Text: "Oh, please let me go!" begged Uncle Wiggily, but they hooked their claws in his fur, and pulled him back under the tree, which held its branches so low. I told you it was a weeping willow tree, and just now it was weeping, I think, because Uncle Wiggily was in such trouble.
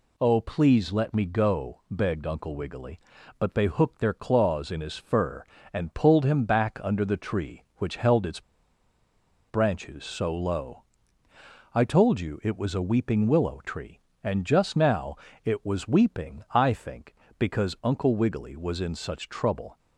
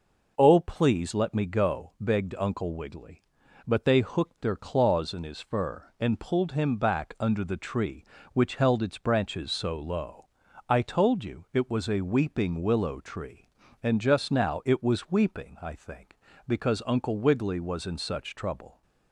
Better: second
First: pauses between "its" and "branches"; at 8.4 s; 1.0 s long // pauses between "now" and "it"; slight; at 15.1 s; 0.30 s long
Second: none

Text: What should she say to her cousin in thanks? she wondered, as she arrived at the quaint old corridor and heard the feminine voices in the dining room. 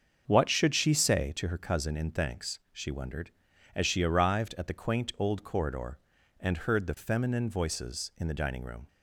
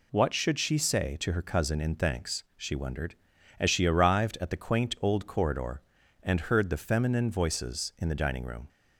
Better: second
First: starts louder than the rest; until 1.4 s; 7 dB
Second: none

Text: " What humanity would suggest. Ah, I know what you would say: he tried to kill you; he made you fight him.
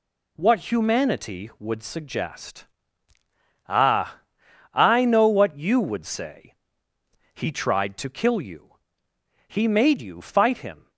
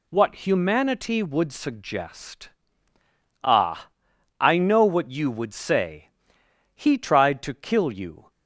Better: first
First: none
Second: stops before "he made you fight him"; at 8.2 s

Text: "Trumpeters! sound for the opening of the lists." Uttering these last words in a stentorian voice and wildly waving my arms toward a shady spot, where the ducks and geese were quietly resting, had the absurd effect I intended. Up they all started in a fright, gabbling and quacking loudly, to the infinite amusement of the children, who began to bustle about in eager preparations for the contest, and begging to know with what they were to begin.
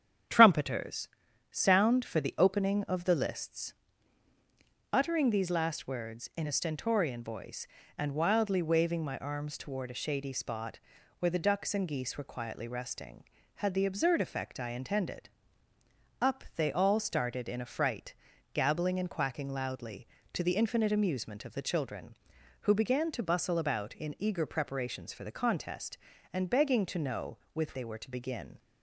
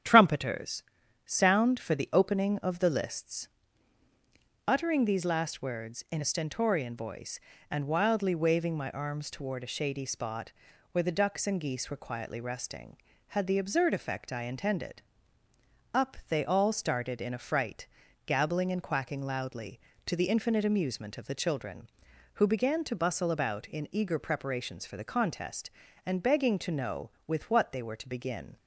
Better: second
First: starts louder than the rest; strong; until 1.7 s; 9 dB // skips "what"; at 27.7 s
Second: starts louder than the rest; strong; until 1.4 s; 9 dB

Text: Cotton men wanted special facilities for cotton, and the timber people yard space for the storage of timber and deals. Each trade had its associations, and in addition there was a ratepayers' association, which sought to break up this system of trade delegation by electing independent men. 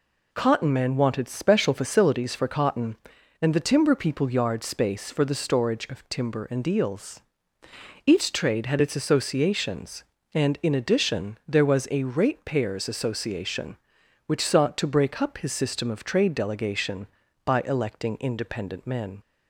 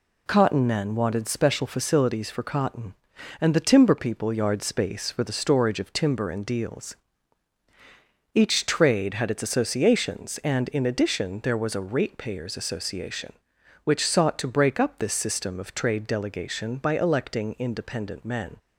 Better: second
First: says "his" for "this"; at 15.3 s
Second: none

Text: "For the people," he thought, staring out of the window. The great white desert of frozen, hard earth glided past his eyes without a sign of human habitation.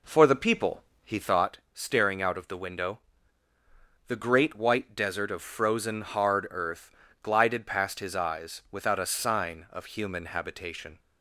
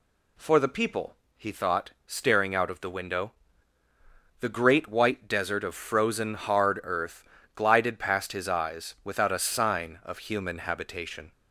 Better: second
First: starts louder than the rest; until 1.5 s; 3.5 dB // pauses between "earth" and "glided"; slight; at 6.9 s; 0.32 s long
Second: pauses between "earth" and "glided"; slight; at 7.2 s; 0.32 s long

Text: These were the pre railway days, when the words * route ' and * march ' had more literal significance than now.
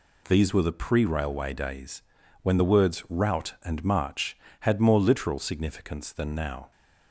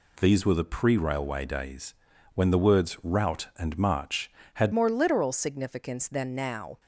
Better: first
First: none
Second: changes voice at "more"; from 4.7 s on; 2.0 s long

